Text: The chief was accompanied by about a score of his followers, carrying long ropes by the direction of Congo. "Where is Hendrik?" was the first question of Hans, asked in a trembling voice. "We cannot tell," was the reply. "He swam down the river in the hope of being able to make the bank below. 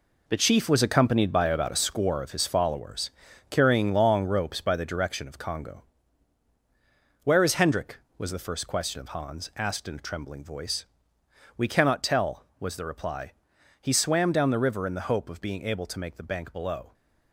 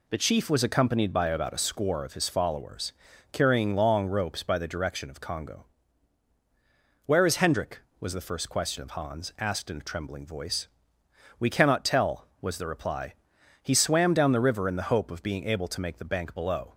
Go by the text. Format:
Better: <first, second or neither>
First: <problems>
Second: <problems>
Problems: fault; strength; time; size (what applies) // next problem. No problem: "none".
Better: second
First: gets quieter; strong; throughout; 9 dB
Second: none